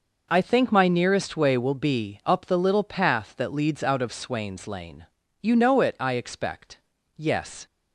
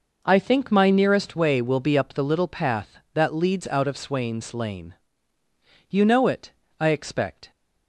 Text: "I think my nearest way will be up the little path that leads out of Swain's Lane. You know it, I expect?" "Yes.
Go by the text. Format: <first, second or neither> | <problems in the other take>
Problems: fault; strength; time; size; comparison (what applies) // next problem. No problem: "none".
first | stops before "Yes"; at 7.5 s